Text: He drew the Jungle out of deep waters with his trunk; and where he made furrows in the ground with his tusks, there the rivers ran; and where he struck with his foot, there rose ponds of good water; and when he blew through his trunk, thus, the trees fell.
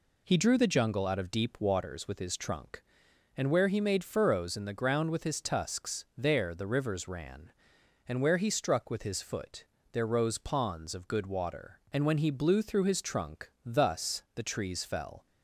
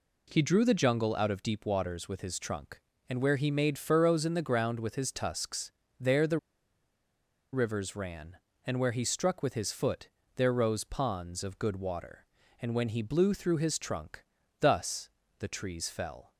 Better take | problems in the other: first | pauses between "the" and "rivers"; at 6.3 s; 1.1 s long

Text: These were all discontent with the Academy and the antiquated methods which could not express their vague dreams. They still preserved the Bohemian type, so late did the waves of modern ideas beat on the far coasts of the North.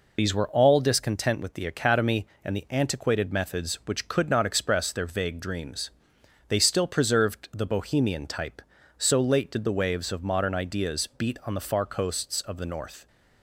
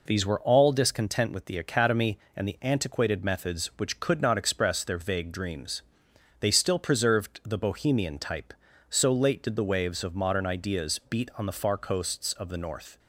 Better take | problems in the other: second | loses the start of "These"; at 0.1 s; 45 ms

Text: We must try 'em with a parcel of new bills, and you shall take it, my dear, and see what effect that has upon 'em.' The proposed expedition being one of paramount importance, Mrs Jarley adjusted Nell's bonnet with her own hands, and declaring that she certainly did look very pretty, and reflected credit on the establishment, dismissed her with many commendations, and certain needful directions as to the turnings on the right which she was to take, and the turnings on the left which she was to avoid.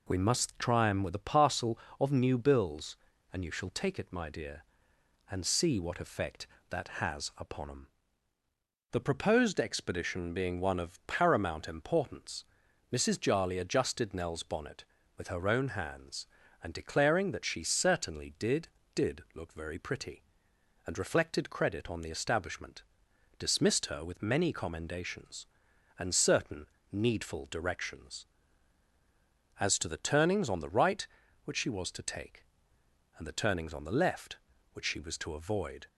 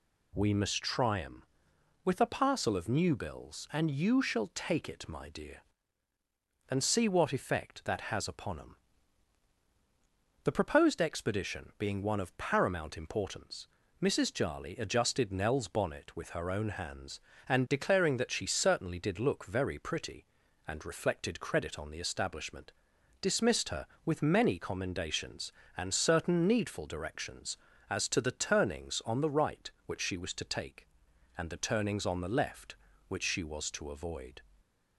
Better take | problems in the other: second | says "did" twice; at 18.9 s // pauses between "certain" and "needful"; slight; at 26.6 s; 0.24 s long

